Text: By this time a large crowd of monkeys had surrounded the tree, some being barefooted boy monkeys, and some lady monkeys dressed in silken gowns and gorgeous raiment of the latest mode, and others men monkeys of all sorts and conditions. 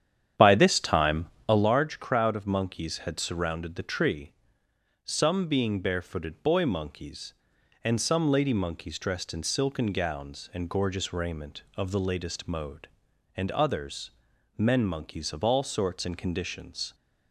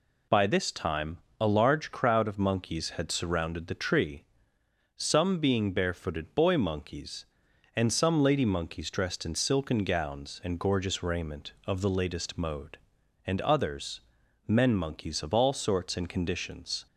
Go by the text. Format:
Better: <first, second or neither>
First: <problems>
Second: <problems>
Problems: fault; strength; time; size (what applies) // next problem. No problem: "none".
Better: second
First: starts louder than the rest; strong; until 1.7 s; 9.5 dB // pauses between "time" and "a"; slight; at 1.2 s; 0.22 s long // pauses between "others" and "men"; noticeable; at 14.1 s; 0.48 s long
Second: pauses between "time" and "a"; slight; at 1.1 s; 0.22 s long // pauses between "others" and "men"; noticeable; at 14.0 s; 0.48 s long